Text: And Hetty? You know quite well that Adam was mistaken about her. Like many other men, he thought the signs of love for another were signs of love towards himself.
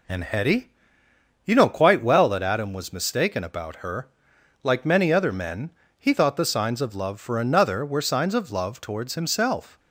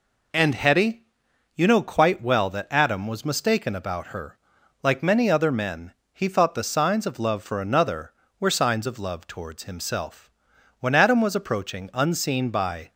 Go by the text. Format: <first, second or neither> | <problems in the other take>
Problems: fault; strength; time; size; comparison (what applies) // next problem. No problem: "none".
first | goes on to say "When Adam was approaching unseen by"; strong; from 10.7 s on; 2.1 s long